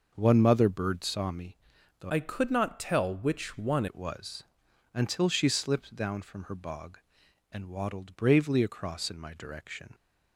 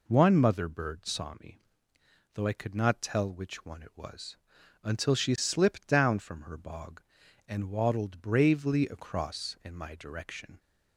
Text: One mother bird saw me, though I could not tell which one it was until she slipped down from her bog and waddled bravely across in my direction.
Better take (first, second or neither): second